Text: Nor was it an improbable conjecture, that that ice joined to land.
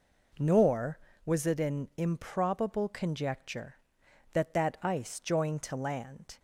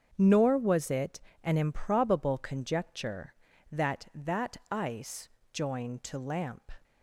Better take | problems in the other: first | starts louder than the rest; strong; until 1.1 s; 7 dB // pauses between "it" and "an"; slight; at 1.2 s; 0.22 s long // pauses between "ice" and "joined"; slight; at 5.3 s; 0.24 s long // says "lamp" for "land"; at 6.1 s

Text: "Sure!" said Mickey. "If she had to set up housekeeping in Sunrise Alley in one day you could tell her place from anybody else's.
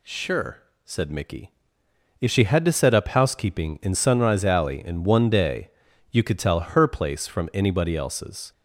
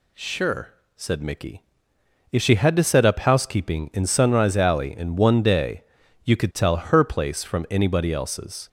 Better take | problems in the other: neither | pauses between "day" and "you"; the same in both

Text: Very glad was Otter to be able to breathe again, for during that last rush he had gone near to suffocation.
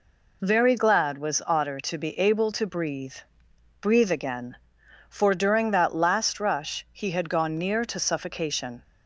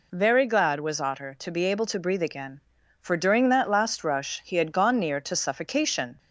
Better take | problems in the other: second | says "breathe" twice; at 3.8 s

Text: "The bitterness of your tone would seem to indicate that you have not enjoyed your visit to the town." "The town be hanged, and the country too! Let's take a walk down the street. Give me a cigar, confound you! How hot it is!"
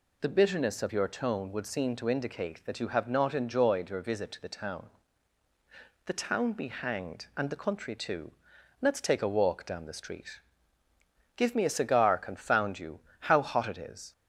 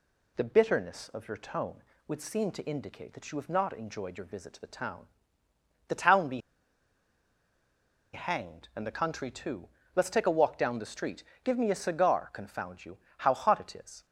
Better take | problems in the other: first | pauses between "be" and "hanged"; strong; at 6.4 s; 1.7 s long

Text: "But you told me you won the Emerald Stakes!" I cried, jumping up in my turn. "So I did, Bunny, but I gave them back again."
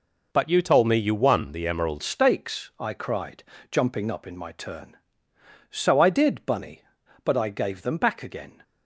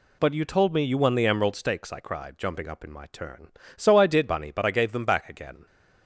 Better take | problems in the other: second | changes voice at "Stakes"; from 2.0 s on; 6.6 s long

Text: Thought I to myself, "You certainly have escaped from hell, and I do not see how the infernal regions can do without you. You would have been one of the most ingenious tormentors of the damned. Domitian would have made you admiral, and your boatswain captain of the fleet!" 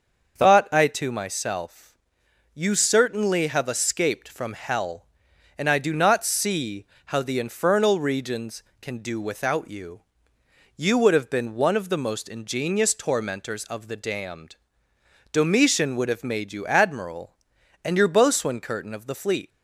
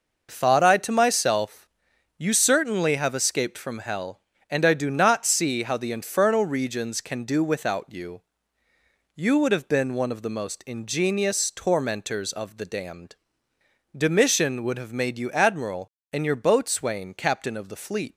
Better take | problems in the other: second | starts louder than the rest; until 1.4 s; 6.5 dB // pauses between "see" and "how"; slight; at 6.8 s; 0.22 s long // says "curtain" for "captain"; at 18.6 s

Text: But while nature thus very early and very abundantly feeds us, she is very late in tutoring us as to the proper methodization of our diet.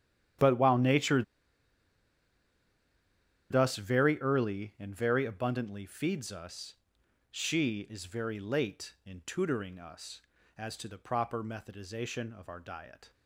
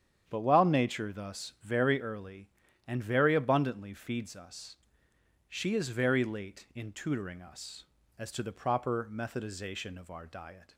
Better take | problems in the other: second | starts louder than the rest; strong; until 3.6 s; 10.5 dB; strong in the second // pauses between "nature" and "thus"; strong; at 1.2 s; 2.2 s long

